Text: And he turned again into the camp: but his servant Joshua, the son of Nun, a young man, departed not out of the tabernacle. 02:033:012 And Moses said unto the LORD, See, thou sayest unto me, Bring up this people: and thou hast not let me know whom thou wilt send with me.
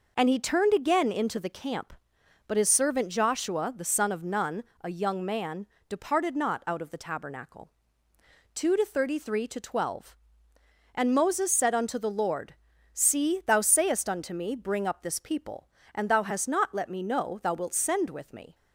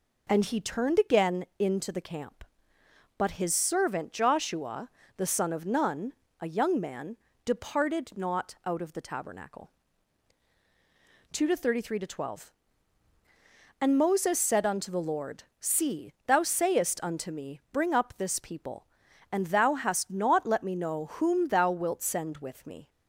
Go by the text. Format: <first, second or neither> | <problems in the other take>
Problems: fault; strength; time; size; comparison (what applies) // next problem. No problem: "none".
second | skips "whom"; at 17.4 s